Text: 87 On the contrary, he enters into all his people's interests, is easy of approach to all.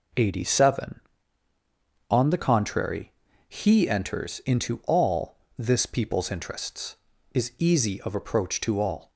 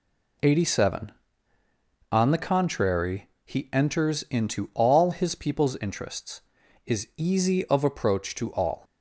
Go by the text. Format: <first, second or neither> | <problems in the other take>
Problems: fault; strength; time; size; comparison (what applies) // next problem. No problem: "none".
second | says "this" for "his"; at 5.5 s